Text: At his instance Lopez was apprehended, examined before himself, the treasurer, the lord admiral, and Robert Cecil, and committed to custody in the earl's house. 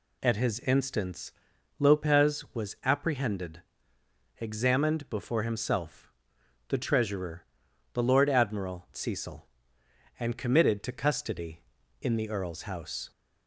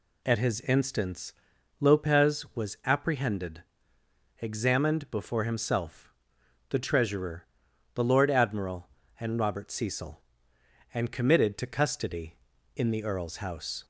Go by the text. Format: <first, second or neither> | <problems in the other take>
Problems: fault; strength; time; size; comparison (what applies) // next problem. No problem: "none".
second | pauses between "instance" and "Lopez"; noticeable; at 1.3 s; 0.48 s long; noticeable in the second // skips "and Robert"; at 8.9 s